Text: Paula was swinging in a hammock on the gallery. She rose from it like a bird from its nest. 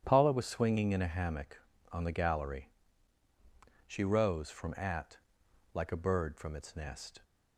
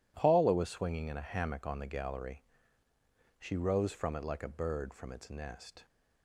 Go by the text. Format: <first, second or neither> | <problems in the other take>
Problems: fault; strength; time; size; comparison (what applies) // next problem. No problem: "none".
second | starts louder than the rest; strong; until 1.0 s; 9.5 dB // says "at" for "it"; at 4.7 s